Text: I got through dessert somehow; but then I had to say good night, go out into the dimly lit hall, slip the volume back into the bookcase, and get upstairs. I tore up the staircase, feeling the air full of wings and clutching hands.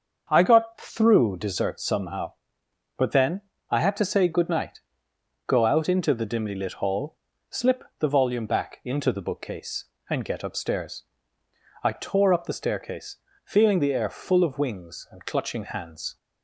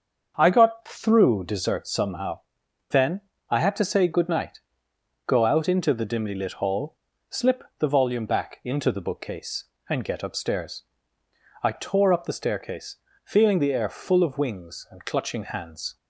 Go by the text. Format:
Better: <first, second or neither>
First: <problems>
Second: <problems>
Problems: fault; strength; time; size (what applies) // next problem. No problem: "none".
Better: first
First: starts louder than the rest; until 1.3 s; 6.5 dB // pauses between "then" and "I"; slight; at 3.4 s; 0.28 s long // pauses between "slip" and "the"; slight; at 7.8 s; 0.16 s long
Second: starts louder than the rest; until 1.3 s; 6.5 dB // skips "but"; at 2.6 s // pauses between "then" and "I"; slight; at 3.2 s; 0.28 s long // pauses between "slip" and "the"; slight; at 7.6 s; 0.16 s long